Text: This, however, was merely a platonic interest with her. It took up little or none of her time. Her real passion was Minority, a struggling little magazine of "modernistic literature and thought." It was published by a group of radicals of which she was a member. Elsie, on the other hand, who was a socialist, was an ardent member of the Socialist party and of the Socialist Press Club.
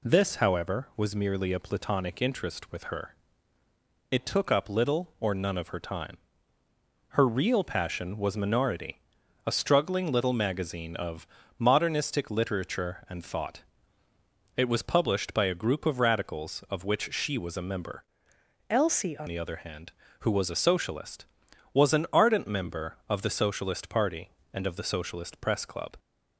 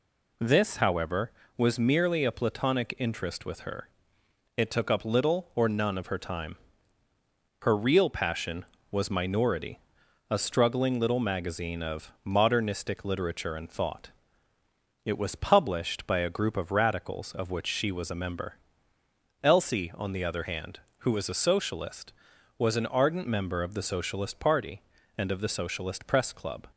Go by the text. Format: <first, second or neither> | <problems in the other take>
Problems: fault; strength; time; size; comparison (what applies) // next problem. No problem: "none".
second | pauses between "of" and "modernistic"; slight; at 11.2 s; 0.32 s long // changes voice from "Elsie" to "on"; from 18.6 to 19.2 s; 0.6 s long